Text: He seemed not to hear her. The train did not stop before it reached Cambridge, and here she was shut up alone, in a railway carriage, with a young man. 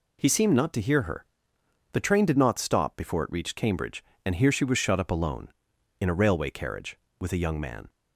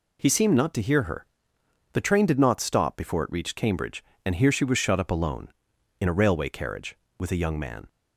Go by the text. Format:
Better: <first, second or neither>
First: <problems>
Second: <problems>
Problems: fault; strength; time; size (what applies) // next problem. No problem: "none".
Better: neither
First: none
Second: none